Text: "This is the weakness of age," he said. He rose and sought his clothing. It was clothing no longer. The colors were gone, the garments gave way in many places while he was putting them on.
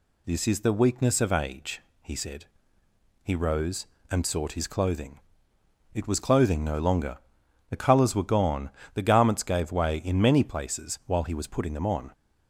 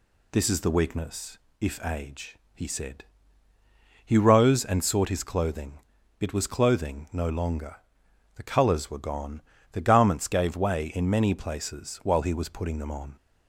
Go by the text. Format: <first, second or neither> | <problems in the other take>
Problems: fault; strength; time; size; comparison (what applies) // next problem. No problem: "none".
first | says "if" for "of"; at 1.6 s